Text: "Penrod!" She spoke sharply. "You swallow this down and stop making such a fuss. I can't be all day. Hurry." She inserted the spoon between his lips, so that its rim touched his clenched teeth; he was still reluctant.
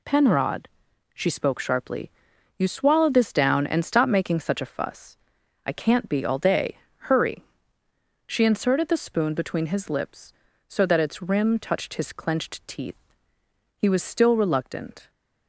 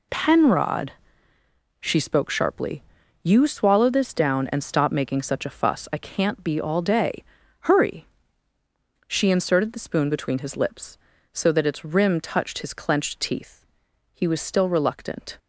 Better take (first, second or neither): neither